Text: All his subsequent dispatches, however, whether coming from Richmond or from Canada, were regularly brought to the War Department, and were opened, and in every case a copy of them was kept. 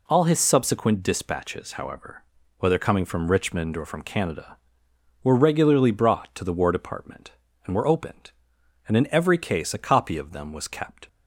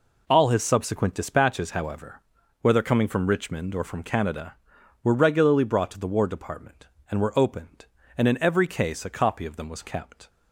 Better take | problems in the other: neither | none

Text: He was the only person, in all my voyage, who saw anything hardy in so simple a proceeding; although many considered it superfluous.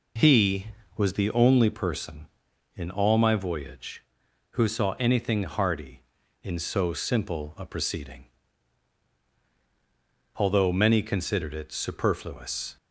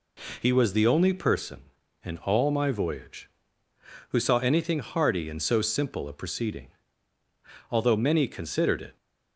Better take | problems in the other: first | stops before "superfluous"; at 8.9 s

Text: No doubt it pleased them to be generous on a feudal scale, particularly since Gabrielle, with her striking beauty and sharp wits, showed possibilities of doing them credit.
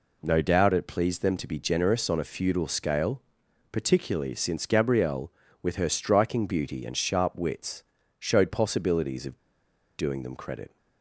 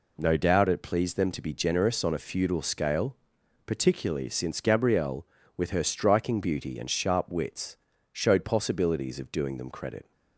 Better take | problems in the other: second | pauses between "of" and "doing"; noticeable; at 9.3 s; 0.59 s long

